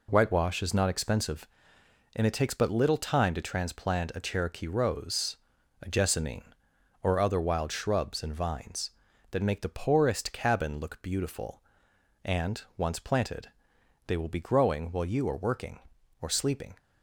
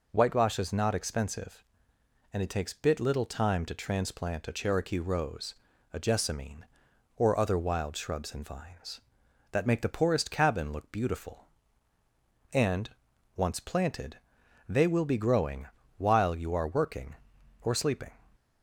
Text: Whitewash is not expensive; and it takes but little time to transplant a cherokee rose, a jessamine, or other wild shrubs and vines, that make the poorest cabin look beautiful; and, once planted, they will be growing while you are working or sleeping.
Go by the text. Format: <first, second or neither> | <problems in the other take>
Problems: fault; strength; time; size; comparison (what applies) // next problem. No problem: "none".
first | says "bit" for "but"; at 2.7 s // pauses between "growing" and "while"; slight; at 15.6 s; 0.32 s long